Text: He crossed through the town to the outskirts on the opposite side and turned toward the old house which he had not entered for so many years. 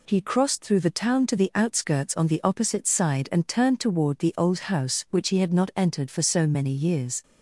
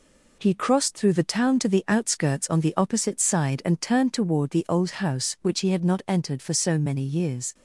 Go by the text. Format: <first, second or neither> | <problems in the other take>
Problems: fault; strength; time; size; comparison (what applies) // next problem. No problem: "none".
first | gets quieter; slight; throughout; 3 dB